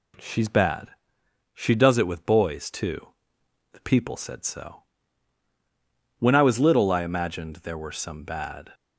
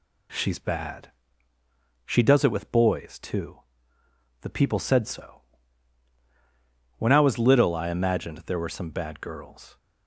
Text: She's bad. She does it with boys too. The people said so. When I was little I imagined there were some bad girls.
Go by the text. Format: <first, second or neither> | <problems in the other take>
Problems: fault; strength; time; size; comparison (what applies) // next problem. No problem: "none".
second | stops before "girls"; at 8.7 s